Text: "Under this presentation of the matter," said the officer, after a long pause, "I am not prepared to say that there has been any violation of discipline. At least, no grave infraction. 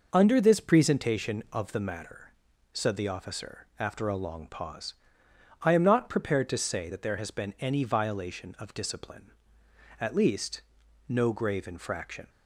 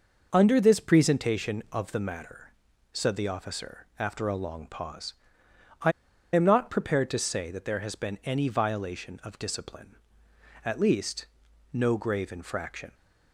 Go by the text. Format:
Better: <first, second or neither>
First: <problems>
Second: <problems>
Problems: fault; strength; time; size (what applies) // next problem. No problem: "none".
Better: first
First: none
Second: pauses between "I" and "am"; at 5.9 s; 0.42 s long